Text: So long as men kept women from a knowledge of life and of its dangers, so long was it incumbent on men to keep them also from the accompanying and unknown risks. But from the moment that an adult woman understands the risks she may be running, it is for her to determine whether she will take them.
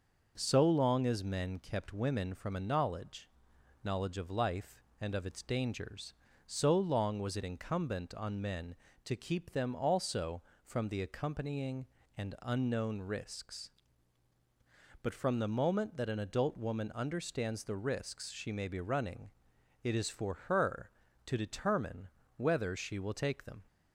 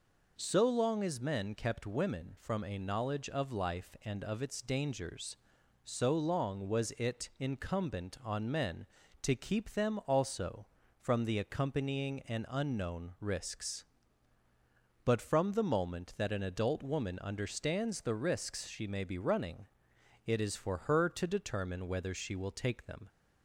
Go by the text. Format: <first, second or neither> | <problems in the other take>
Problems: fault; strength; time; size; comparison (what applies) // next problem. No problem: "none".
second | says "knowledge" twice; at 3.8 s // pauses between "determine" and "whether"; slight; at 22.0 s; 0.28 s long